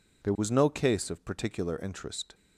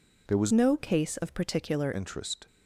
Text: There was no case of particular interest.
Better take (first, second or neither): first